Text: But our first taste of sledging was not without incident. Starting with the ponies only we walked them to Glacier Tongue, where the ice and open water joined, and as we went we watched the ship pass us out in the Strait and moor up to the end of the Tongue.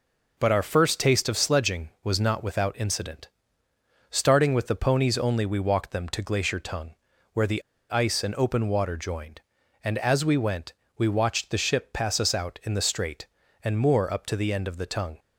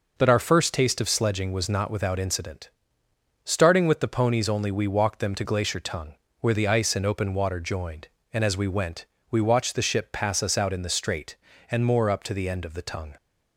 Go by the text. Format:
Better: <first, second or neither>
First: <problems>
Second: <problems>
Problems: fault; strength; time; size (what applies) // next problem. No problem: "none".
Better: second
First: pauses between "the" and "ice"; slight; at 7.6 s; 0.28 s long // pauses between "went" and "we"; slight; at 10.7 s; 0.24 s long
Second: pauses between "went" and "we"; slight; at 9.0 s; 0.26 s long